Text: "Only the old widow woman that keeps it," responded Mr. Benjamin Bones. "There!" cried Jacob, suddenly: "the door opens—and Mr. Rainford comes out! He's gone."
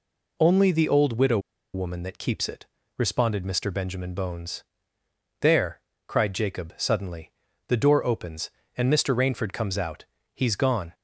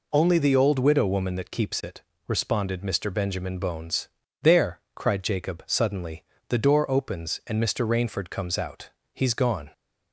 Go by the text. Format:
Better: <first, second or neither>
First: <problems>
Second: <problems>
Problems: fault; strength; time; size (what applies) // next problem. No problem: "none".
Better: second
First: pauses between "widow" and "woman"; slight; at 1.3 s; 0.35 s long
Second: none